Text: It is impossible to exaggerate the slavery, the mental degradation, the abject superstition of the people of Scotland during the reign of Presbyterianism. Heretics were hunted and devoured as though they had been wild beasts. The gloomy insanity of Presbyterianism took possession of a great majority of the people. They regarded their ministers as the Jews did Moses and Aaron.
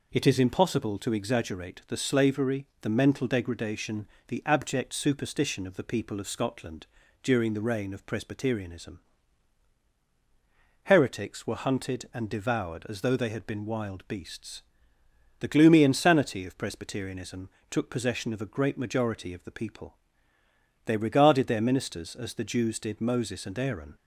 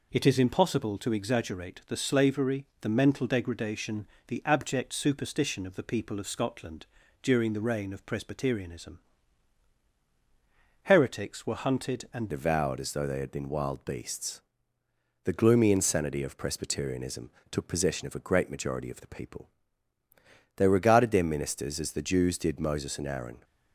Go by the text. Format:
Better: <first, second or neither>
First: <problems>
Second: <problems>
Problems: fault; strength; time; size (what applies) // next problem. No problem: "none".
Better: first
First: pauses between "Scotland" and "during"; slight; at 6.8 s; 0.36 s long // pauses between "Presbyterianism" and "took"; slight; at 17.4 s; 0.20 s long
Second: pauses between "Scotland" and "during"; slight; at 6.8 s; 0.36 s long // changes voice at "devoured"; from 12.2 s on; 11.2 s long // pauses between "Presbyterianism" and "took"; slight; at 17.2 s; 0.22 s long